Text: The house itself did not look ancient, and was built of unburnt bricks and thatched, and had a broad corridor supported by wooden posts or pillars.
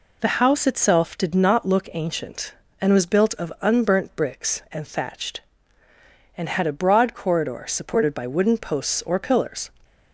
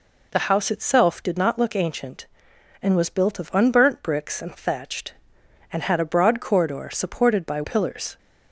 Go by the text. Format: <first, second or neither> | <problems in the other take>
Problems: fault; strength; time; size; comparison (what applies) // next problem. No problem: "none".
first | skips "wooden posts or"; at 7.6 s